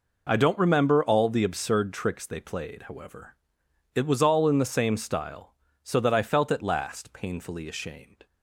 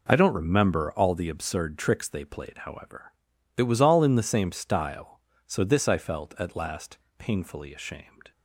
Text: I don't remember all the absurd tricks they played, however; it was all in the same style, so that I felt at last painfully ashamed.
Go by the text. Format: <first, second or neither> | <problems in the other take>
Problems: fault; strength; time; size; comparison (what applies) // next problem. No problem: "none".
first | says "this" for "that"; at 5.6 s // pauses between "last" and "painfully"; slight; at 6.9 s; 0.22 s long